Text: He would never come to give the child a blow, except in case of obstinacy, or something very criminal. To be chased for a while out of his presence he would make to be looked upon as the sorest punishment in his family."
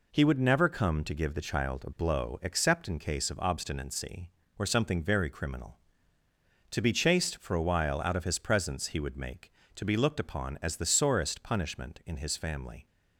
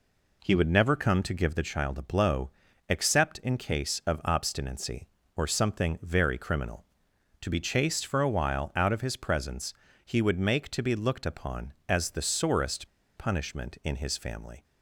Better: first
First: none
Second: pauses between "presence" and "he"; slight; at 9.7 s; 0.32 s long // pauses between "sorest" and "punishment"; slight; at 12.8 s; 0.29 s long

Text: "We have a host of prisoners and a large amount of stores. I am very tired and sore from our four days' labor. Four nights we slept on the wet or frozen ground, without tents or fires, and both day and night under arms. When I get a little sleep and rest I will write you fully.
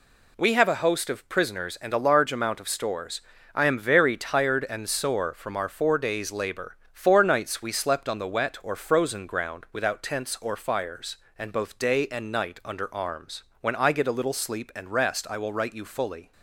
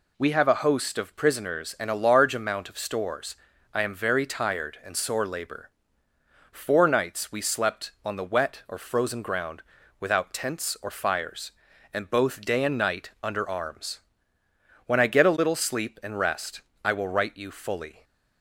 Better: first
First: none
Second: skips "from our four days"; at 5.2 s // pauses between "rest" and "I"; slight; at 16.6 s; 0.20 s long

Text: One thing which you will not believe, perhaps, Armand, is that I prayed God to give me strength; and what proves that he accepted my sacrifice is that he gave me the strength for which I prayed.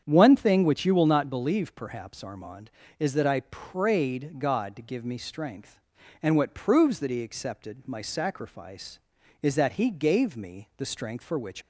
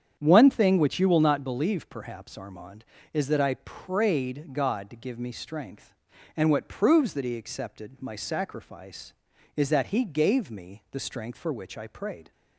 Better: second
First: starts louder than the rest; strong; until 1.0 s; 8 dB // stops before "I prayed"; at 11.6 s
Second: starts louder than the rest; strong; until 1.2 s; 8.5 dB

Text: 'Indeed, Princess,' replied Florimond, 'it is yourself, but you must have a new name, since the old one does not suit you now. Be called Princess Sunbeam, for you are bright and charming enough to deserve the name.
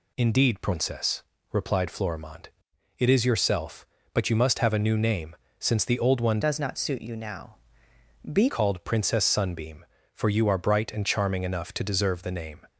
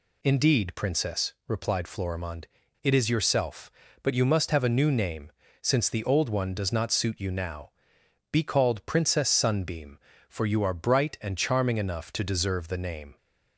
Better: second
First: changes voice from "does" to "Be"; from 6.4 to 8.4 s; 2.0 s long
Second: none

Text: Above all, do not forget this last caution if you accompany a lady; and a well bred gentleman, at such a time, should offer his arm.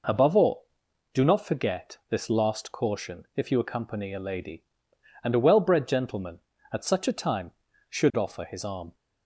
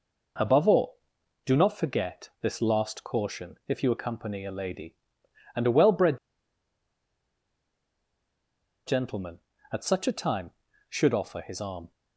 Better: first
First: none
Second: pauses between "bred" and "gentleman"; strong; at 6.1 s; 2.6 s long

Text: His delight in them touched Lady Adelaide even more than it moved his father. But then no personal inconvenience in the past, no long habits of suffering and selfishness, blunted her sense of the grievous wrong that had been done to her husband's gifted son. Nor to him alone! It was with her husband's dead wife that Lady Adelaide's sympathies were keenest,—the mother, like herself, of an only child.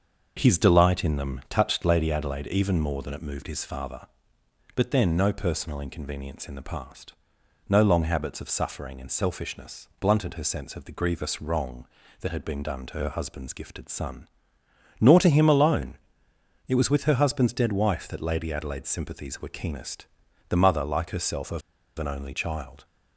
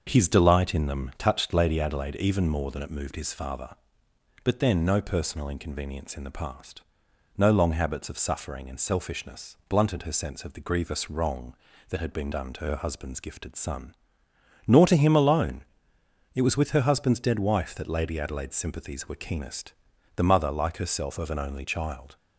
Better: second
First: starts louder than the rest; until 1.3 s; 6.5 dB // pauses between "of" and "an"; at 21.6 s; 0.38 s long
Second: starts louder than the rest; until 1.0 s; 6.5 dB

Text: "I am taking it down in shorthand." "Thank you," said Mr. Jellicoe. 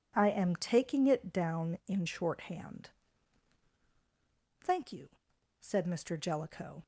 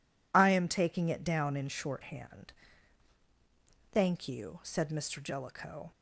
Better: neither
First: none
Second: none

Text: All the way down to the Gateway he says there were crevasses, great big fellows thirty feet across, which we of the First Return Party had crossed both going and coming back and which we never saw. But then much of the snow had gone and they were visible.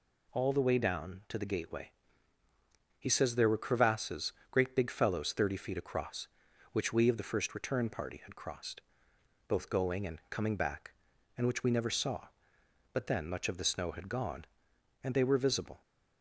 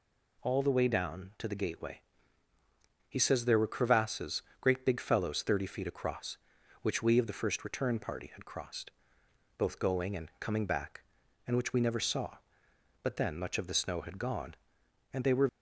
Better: first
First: pauses between "Gateway" and "he"; at 1.8 s; 1.1 s long // pauses between "crossed" and "both"; noticeable; at 8.7 s; 0.68 s long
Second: pauses between "Gateway" and "he"; at 1.9 s; 1.1 s long // pauses between "crossed" and "both"; noticeable; at 8.8 s; 0.68 s long // stops before "visible"; at 15.4 s

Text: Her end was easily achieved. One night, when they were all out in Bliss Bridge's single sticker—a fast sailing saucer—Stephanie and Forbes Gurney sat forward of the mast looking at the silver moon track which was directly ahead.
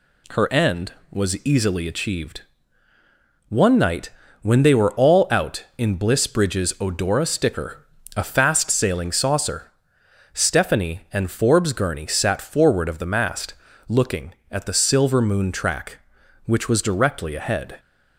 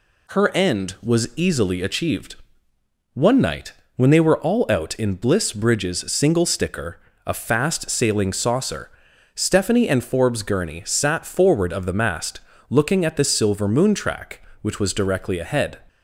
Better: second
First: says "odora" for "single"; at 6.7 s // pauses between "mast" and "looking"; slight; at 13.5 s; 0.34 s long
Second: pauses between "mast" and "looking"; slight; at 12.3 s; 0.30 s long

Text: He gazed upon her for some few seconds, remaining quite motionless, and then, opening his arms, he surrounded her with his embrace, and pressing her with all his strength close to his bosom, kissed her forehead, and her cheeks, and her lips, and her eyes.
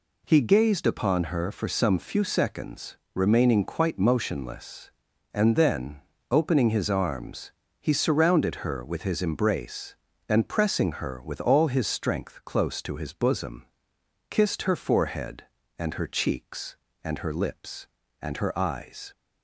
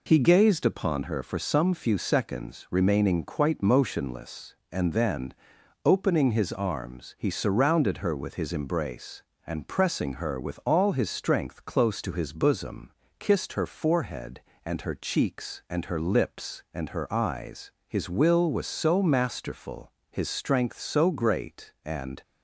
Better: first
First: none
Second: goes on to say "His will was so masterful his strength so great and"; strong; from 17.8 s on; 4.3 s long

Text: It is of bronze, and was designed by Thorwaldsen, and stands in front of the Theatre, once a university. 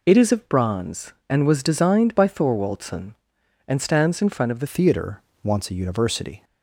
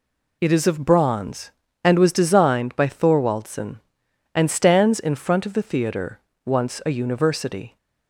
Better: second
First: changes voice at "Theatre"; from 4.6 s on; 1.8 s long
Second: none

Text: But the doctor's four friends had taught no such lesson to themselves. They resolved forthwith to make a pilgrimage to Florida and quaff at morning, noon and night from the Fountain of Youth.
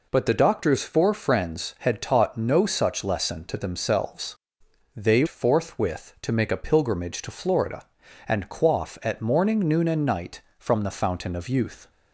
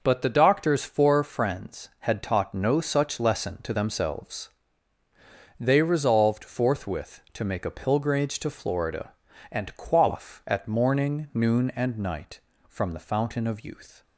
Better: second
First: skips "resolved"; at 5.2 s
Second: none

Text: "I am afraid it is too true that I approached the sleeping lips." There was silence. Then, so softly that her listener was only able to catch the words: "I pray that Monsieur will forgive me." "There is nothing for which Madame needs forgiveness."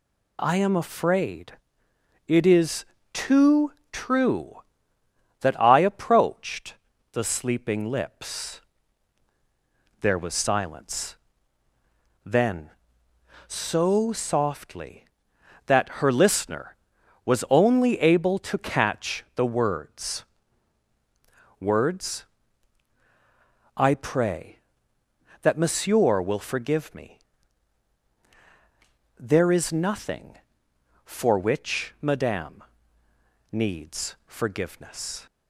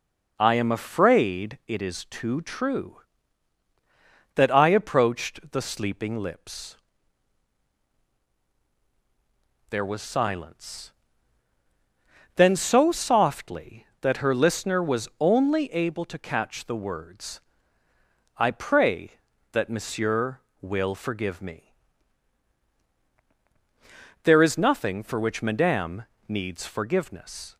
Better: second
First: pauses between "afraid" and "it"; noticeable; at 1.5 s; 0.68 s long // pauses between "is" and "too"; slight; at 2.8 s; 0.26 s long // pauses between "too" and "true"; slight; at 3.7 s; 0.20 s long // pauses between "approached" and "the"; slight; at 6.7 s; 0.36 s long // says "words" twice; at 21.5 s // pauses between "Madame" and "needs"; noticeable; at 32.6 s; 0.88 s long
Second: pauses between "Madame" and "needs"; slight; at 26.0 s; 0.20 s long

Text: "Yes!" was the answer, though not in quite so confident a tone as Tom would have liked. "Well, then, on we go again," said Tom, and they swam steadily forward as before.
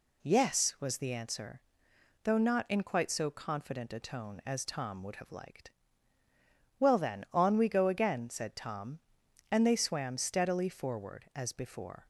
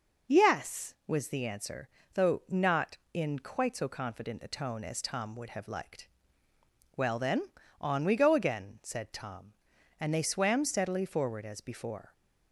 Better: neither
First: none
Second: none

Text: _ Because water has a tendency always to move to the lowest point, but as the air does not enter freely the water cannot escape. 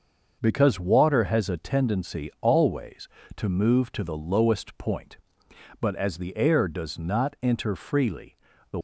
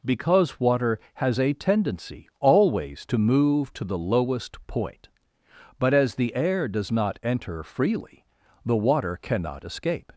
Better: second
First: starts louder than the rest; until 1.4 s; 6.5 dB // pauses between "freely" and "the"; slight; at 8.3 s; 0.34 s long // stops before "water cannot escape"; at 8.7 s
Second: pauses between "freely" and "the"; at 8.2 s; 0.40 s long

